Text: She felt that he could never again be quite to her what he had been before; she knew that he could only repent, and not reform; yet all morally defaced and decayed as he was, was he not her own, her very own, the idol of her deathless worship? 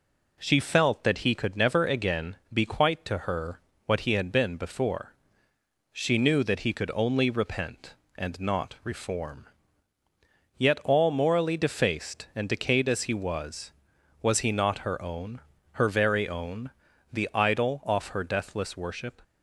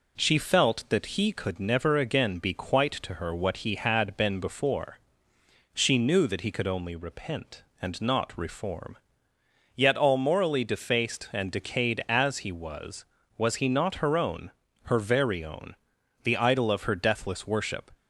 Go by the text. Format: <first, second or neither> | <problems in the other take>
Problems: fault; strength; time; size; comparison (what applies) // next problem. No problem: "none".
second | pauses between "again" and "be"; slight; at 2.3 s; 0.16 s long // pauses between "her" and "what"; slight; at 3.5 s; 0.26 s long // says "off" for "of"; at 17.8 s